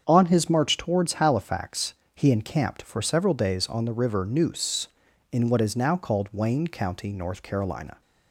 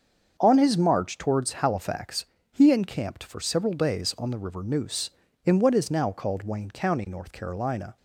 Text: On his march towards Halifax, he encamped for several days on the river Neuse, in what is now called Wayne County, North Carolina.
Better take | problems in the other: neither | starts louder than the rest; the same in both

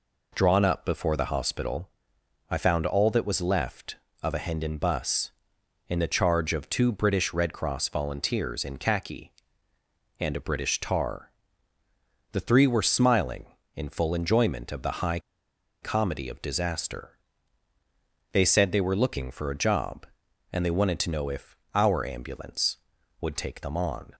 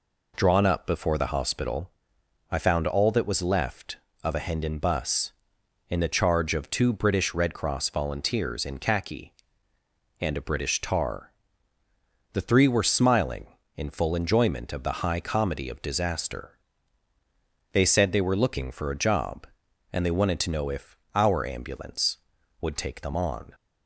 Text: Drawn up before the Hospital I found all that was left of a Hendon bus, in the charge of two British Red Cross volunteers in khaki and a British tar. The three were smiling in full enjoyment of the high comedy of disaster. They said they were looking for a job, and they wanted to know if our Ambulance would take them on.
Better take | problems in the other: second | pauses between "Hospital" and "I"; noticeable; at 1.8 s; 0.60 s long; noticeable in the second // pauses between "high" and "comedy"; noticeable; at 15.1 s; 0.62 s long // pauses between "if" and "our"; slight; at 21.5 s; 0.18 s long; slight in the second

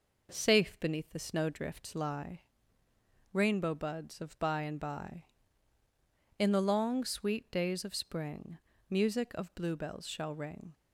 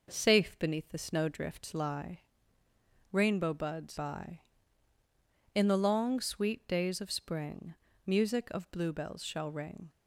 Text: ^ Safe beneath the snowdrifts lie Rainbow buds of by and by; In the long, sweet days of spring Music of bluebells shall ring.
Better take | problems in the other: first | pauses between "lie" and "Rainbow"; noticeable; at 2.2 s; 0.90 s long; noticeable in the first // skips "of by and"; at 3.9 s // pauses between "spring" and "Music"; slight; at 7.7 s; 0.34 s long; slight in the first

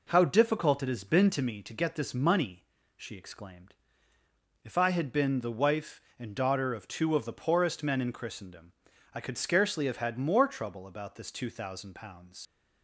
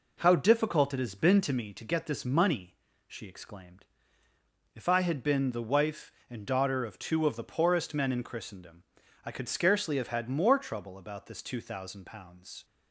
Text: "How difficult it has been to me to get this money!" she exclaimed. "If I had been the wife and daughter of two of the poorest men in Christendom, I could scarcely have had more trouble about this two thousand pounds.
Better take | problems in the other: second | leaves "pounds" unfinished; at 12.4 s; 85 ms

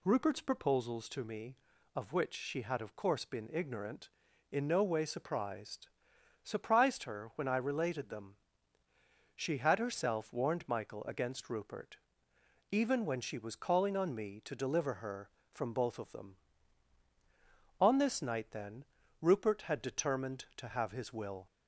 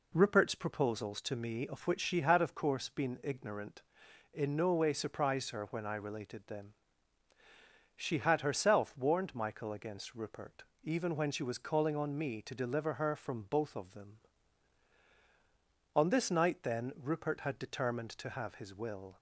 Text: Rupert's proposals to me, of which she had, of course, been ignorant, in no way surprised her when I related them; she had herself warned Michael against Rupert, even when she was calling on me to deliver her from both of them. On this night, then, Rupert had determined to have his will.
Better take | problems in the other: second | says "surprised" twice; at 6.4 s

